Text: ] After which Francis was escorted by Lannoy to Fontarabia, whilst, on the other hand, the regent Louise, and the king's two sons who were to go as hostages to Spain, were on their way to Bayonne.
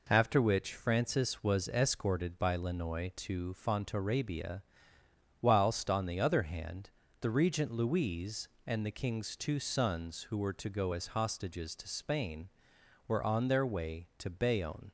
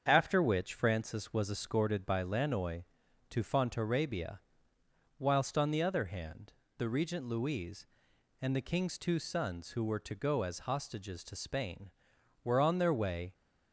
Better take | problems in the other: first | starts louder than the rest; strong; until 1.0 s; 7 dB // stops before "to Bayonne"; at 13.3 s

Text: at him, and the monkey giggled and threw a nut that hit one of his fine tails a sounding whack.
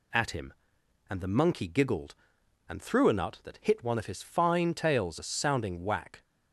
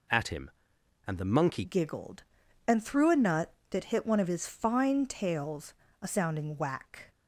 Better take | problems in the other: first | changes voice at "giggled"; from 1.6 s on; 5.5 s long // pauses between "tails" and "a"; slight; at 5.7 s; 0.28 s long

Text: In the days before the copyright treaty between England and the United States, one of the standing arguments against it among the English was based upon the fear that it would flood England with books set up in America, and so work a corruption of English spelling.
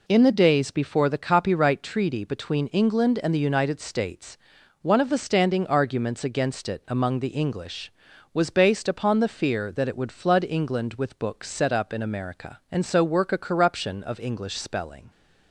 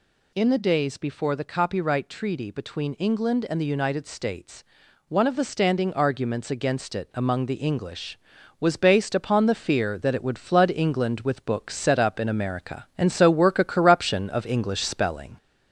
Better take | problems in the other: first | gets louder; slight; throughout; 3 dB

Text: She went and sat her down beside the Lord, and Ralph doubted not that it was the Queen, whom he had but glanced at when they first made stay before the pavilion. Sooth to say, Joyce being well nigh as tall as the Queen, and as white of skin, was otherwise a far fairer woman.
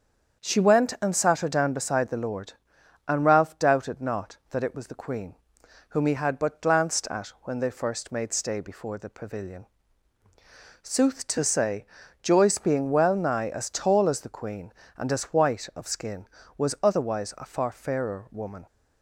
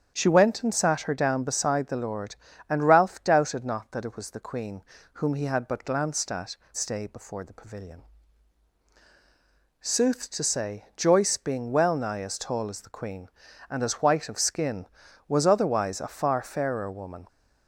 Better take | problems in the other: first | starts louder than the rest; strong; until 1.1 s; 8.5 dB; also in the first // skips "when they first made"; at 6.6 s

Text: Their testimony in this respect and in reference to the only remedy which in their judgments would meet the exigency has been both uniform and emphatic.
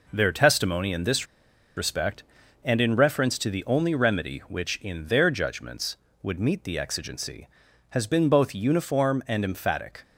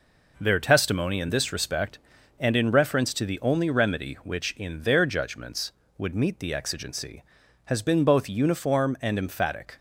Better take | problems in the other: second | pauses between "this" and "respect"; noticeable; at 1.2 s; 0.50 s long

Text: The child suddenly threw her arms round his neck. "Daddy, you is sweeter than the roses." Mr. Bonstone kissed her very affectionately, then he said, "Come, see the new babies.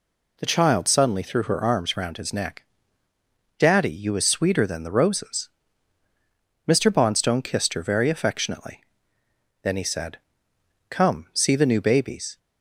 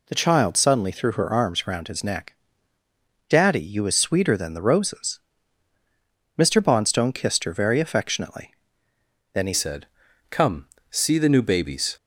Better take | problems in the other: first | changes voice at "said"; from 9.5 s on; 2.4 s long

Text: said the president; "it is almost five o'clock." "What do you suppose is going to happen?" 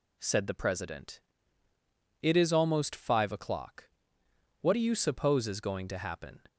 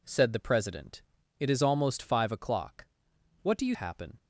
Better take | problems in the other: first | skips "suppose is going to"; at 3.7 s

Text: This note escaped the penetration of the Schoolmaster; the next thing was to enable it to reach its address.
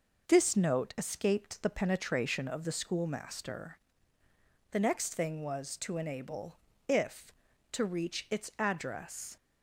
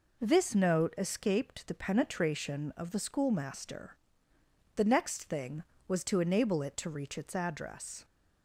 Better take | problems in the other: second | says "if" for "it"; at 6.8 s

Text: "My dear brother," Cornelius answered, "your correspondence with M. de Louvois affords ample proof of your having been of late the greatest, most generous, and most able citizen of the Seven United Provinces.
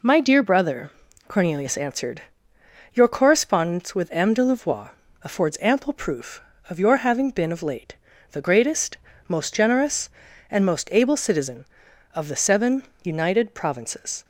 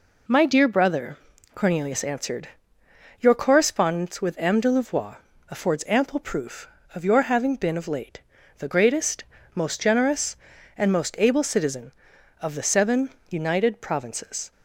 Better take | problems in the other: neither | pauses between "Louvois" and "affords"; slight; the same in both // pauses between "late" and "the"; slight; the same in both // pauses between "Seven" and "United"; slight; the same in both

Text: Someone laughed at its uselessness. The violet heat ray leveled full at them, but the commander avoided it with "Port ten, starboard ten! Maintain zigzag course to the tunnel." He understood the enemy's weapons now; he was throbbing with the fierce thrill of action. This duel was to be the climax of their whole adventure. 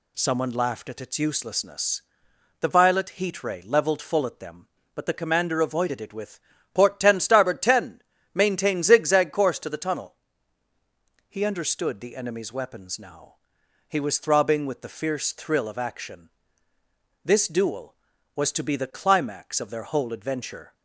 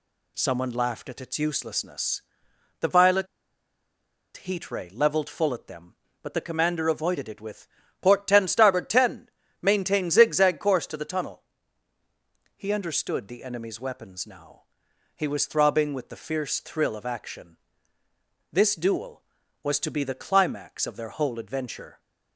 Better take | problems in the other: first | pauses between "violet" and "heat"; at 3.2 s; 1.1 s long // pauses between "with" and "Port"; slight; at 7.6 s; 0.32 s long; slight in the first

